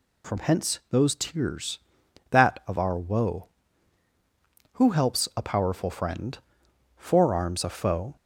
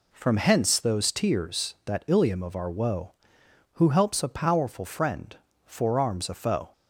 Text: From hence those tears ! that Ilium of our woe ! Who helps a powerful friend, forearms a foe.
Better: second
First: skips "Ilium"; at 2.6 s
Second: none

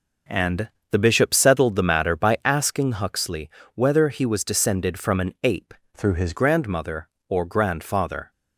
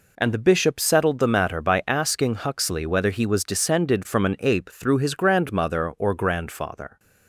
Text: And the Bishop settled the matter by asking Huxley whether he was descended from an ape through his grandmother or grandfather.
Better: second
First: pauses between "And" and "the"; slight; at 0.6 s; 0.22 s long // pauses between "Huxley" and "whether"; slight; at 3.4 s; 0.26 s long // changes voice from "through" to "his"; from 5.9 to 6.3 s; 0.4 s long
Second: none

